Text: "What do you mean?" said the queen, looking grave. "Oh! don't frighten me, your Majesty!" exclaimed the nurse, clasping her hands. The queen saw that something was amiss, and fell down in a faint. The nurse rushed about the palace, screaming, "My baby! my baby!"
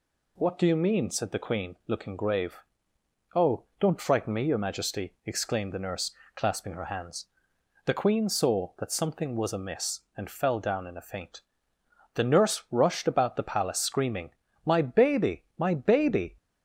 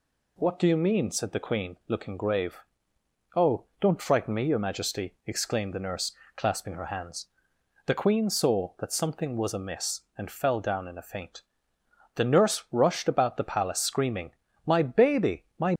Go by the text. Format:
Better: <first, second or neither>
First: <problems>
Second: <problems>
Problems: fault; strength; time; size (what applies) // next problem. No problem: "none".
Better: first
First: none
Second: stops before "baby"; at 15.7 s